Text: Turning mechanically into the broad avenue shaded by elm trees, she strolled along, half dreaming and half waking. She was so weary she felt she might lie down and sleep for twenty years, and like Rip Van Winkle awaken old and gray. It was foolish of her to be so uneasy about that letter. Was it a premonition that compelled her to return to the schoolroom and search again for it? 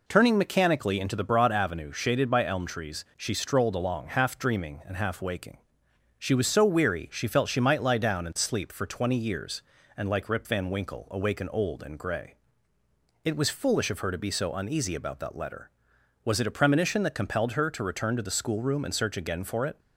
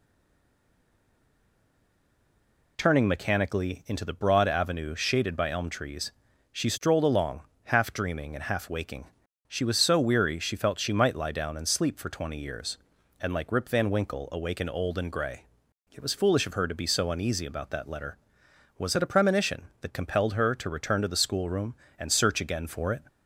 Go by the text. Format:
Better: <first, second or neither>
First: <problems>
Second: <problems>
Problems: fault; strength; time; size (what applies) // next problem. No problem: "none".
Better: first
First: none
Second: stays silent before the first word; strong; until 2.7 s; 2.7 s long